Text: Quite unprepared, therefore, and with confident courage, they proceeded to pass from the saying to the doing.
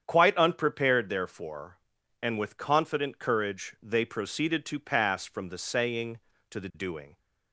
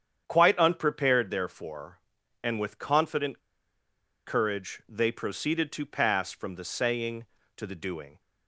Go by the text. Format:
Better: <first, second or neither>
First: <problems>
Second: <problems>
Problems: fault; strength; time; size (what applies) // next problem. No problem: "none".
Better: first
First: starts louder than the rest; strong; until 1.0 s; 8.5 dB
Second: starts louder than the rest; strong; until 1.2 s; 8.5 dB // pauses between "confident" and "courage"; noticeable; at 3.3 s; 0.86 s long